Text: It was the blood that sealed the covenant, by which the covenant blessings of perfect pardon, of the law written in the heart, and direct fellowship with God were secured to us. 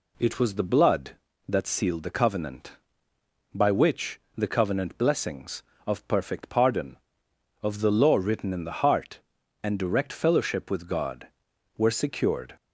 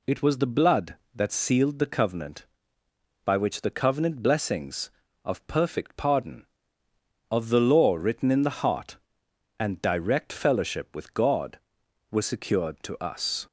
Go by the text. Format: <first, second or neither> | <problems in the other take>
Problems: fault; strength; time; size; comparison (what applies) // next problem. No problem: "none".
second | pauses between "which" and "the"; slight; at 4.2 s; 0.16 s long // stops before "to us"; at 12.5 s